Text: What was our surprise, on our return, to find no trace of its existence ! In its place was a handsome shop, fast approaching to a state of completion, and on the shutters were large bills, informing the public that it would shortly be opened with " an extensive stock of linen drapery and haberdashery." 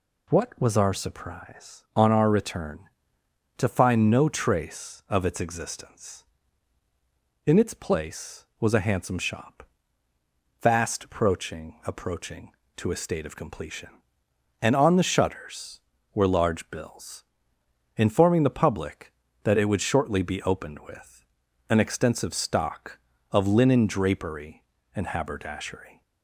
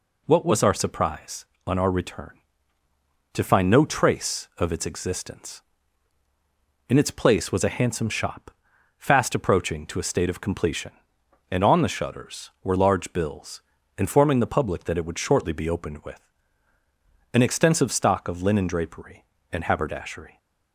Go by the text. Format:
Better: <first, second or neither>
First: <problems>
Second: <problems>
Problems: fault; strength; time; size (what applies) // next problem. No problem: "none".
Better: second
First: says "approaching" twice; at 11.8 s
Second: none